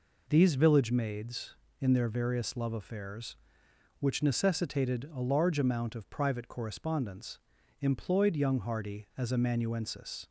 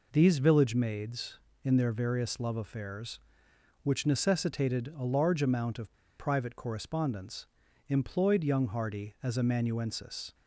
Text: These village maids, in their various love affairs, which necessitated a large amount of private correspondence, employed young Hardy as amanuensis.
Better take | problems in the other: first | pauses between "of" and "private"; slight; at 5.9 s; 0.25 s long

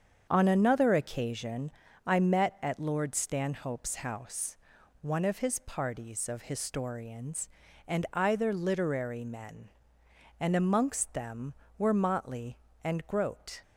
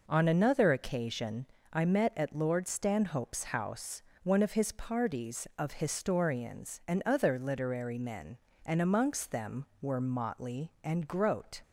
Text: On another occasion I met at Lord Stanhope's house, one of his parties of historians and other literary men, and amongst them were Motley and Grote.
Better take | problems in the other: second | starts louder than the rest; strong; until 1.3 s; 7.5 dB // pauses between "occasion" and "I"; slight; at 1.7 s; 0.34 s long; slight in the second // says "either" for "other"; at 8.1 s

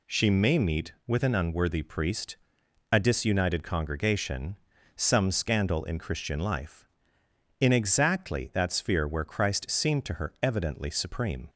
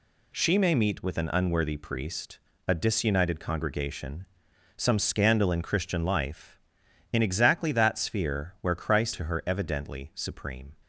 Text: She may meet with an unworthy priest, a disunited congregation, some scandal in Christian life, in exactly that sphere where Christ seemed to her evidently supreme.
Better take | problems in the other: first | skips "seemed"; at 9.1 s

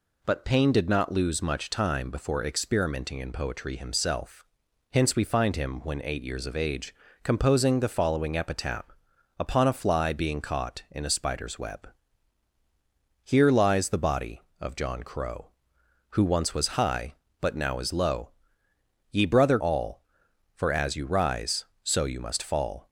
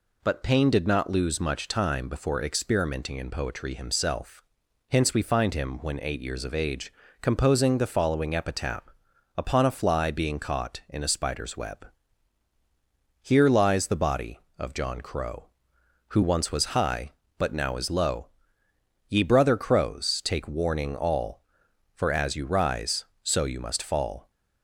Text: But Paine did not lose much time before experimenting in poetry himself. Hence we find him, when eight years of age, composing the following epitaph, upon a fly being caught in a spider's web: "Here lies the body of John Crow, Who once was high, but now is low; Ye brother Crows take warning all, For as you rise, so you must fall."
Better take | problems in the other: second | skips "Crows take warning"; at 19.5 s

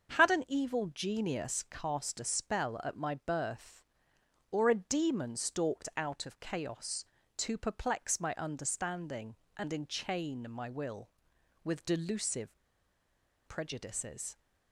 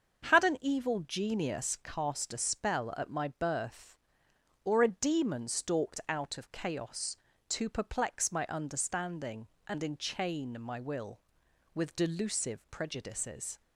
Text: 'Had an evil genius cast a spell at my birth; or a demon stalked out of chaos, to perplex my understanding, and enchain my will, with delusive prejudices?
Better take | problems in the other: second | starts louder than the rest; until 1.2 s; 7 dB; also in the second // pauses between "delusive" and "prejudices"; noticeable; at 12.5 s; 0.88 s long

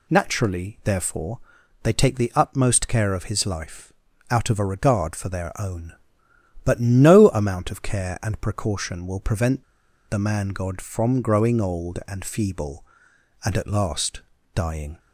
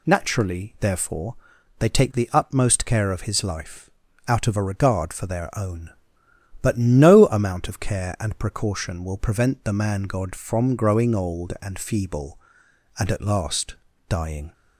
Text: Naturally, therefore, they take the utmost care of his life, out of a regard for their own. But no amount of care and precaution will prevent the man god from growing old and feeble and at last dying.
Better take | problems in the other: second | pauses between "prevent" and "the"; noticeable; at 9.6 s; 0.46 s long // pauses between "last" and "dying"; slight; at 14.2 s; 0.34 s long; slight in the second

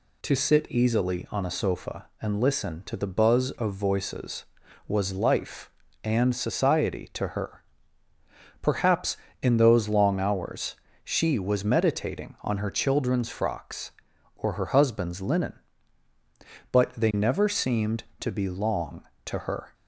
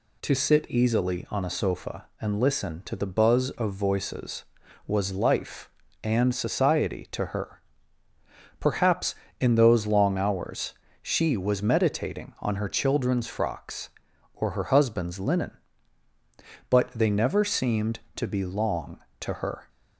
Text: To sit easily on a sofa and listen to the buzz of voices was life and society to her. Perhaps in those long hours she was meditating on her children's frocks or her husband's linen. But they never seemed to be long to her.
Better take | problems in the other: neither | pauses between "hours" and "she"; slight; the same in both

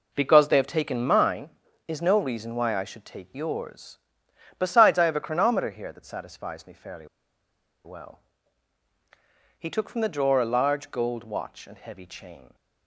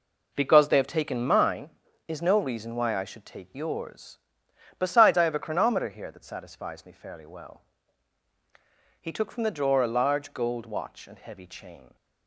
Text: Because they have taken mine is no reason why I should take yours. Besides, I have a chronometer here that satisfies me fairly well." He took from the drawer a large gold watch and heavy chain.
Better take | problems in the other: second | pauses between "fairly" and "well"; noticeable; at 7.0 s; 0.78 s long

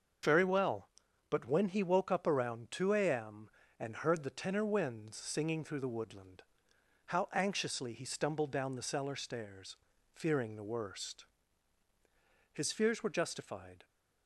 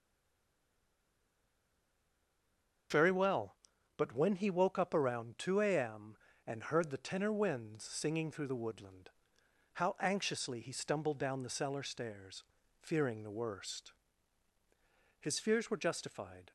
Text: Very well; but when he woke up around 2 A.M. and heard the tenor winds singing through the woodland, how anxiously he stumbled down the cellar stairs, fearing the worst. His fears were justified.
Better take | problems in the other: first | stays silent before the first word; strong; until 2.9 s; 2.9 s long // starts louder than the rest; until 4.3 s; 6.5 dB; also in the first

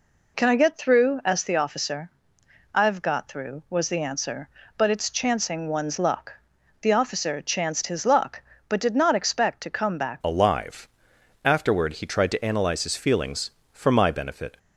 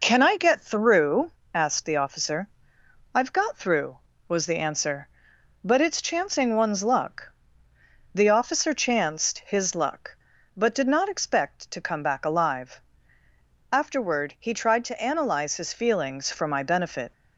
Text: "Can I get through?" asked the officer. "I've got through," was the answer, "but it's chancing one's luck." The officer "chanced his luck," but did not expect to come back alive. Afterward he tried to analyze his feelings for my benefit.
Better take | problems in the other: second | changes voice at "alive"; from 10.2 s on; 4.3 s long

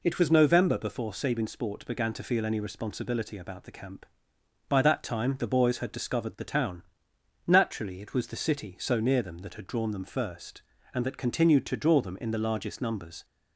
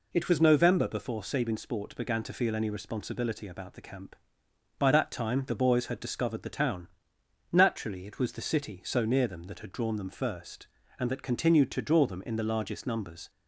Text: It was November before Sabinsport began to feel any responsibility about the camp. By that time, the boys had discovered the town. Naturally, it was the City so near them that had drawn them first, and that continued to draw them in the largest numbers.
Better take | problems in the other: neither | none

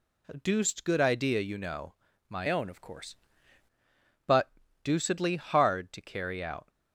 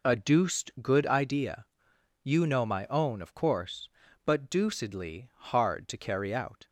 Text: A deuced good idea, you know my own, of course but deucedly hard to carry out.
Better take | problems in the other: second | pauses between "know" and "my"; slight; at 1.9 s; 0.36 s long // changes voice from "own" to "course"; from 2.5 to 3.1 s; 0.6 s long // pauses between "but" and "deucedly"; slight; at 4.5 s; 0.30 s long

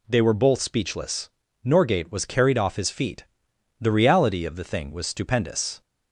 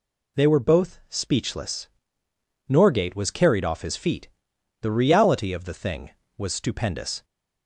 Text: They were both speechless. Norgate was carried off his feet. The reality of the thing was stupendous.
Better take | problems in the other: neither | none

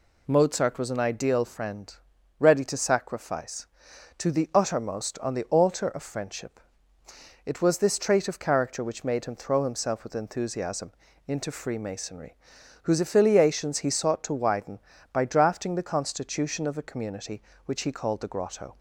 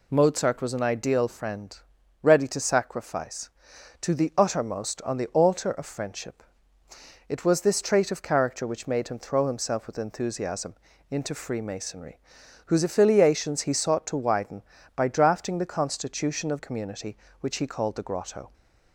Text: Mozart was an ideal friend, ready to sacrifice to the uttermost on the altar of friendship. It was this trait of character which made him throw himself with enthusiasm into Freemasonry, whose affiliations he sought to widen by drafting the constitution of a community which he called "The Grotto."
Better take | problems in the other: first | pauses between "enthusiasm" and "into"; slight; at 10.7 s; 0.36 s long; slight in the first // skips "a"; at 16.5 s

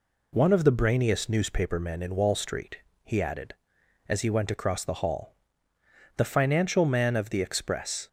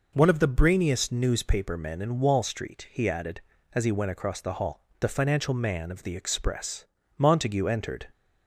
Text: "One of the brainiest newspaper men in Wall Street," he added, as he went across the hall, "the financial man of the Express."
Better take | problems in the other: first | goes on to say "Montague entered"; noticeable; from 7.1 s on; 0.88 s long

